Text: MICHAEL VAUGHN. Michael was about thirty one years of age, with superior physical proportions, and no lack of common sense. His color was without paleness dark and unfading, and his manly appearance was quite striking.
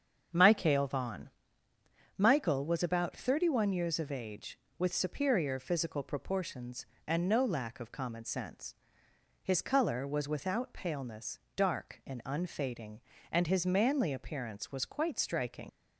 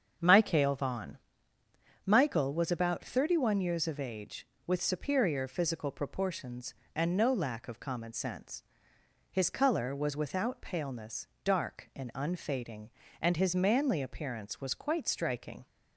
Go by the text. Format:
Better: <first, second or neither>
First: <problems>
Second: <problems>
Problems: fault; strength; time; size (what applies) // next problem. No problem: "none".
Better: second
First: starts louder than the rest; strong; until 2.2 s; 7 dB // pauses between "paleness" and "dark"; slight; at 11.4 s; 0.16 s long // leaves "striking" unfinished; at 15.6 s; 75 ms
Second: starts louder than the rest; strong; until 2.0 s; 7 dB // pauses between "paleness" and "dark"; slight; at 11.2 s; 0.16 s long